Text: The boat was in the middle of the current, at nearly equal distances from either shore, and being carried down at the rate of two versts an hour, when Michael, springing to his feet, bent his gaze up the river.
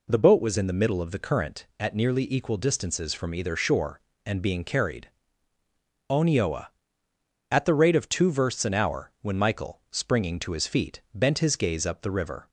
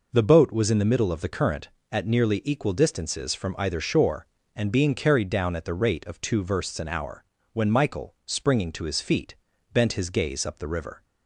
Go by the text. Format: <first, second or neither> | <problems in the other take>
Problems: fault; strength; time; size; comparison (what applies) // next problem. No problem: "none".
second | says "onioa" for "down"; at 6.0 s